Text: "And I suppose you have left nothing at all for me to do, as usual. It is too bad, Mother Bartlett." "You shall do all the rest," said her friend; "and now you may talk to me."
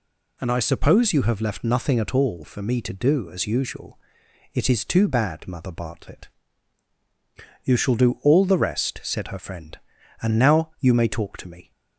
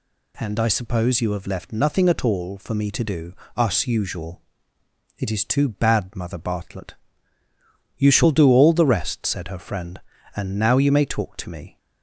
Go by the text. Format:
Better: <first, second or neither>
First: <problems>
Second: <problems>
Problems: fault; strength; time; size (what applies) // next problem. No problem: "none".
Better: first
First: none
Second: says "us" for "as"; at 3.5 s